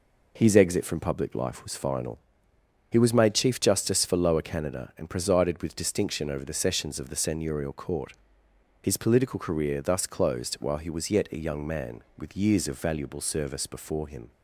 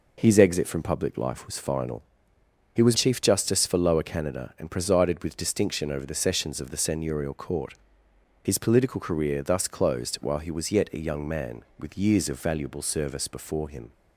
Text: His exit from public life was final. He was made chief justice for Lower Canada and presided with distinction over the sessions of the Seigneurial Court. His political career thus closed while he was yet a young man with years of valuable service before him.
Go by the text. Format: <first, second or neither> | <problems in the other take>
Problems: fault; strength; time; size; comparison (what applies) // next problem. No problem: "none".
first | skips "made"; at 2.9 s